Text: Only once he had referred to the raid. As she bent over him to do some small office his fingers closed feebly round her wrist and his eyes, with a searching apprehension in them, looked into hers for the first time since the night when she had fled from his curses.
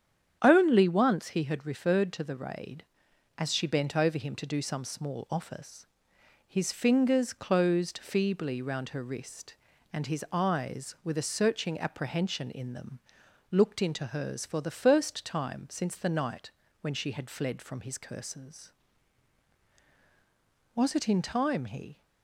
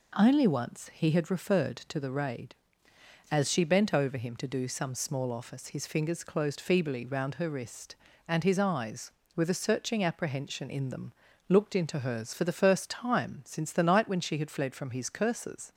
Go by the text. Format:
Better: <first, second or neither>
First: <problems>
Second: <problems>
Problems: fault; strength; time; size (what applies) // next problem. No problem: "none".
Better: second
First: starts louder than the rest; strong; until 1.4 s; 8.5 dB // pauses between "office" and "his"; noticeable; at 5.8 s; 0.60 s long // pauses between "night" and "when"; slight; at 16.5 s; 0.28 s long // goes on to say "Was it in time he"; noticeable; from 20.7 s on; 1.2 s long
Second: none